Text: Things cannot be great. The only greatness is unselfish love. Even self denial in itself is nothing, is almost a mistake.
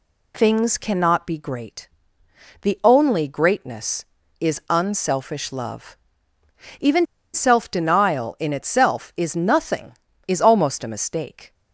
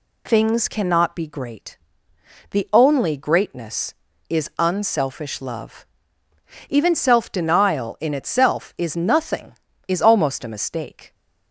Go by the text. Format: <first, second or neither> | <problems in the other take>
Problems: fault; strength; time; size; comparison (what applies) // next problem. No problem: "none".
second | pauses between "Even" and "self"; slight; at 7.0 s; 0.28 s long